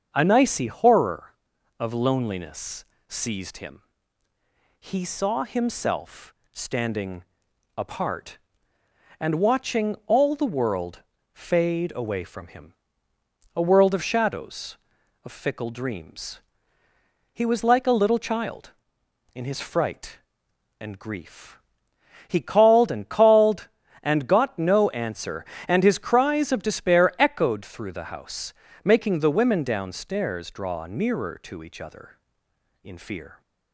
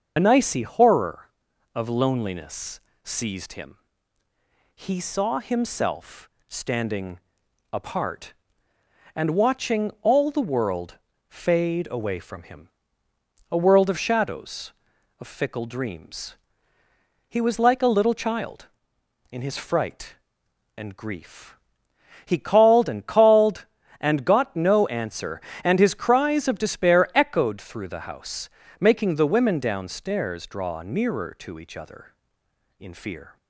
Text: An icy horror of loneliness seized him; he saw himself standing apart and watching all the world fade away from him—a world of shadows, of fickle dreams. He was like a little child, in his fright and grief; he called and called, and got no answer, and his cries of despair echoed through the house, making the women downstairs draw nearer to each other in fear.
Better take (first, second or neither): first